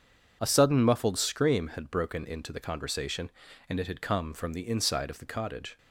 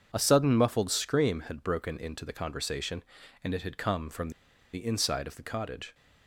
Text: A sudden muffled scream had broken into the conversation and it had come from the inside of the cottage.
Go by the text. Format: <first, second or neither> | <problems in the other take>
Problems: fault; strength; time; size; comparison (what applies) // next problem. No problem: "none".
first | pauses between "from" and "the"; at 4.2 s; 0.43 s long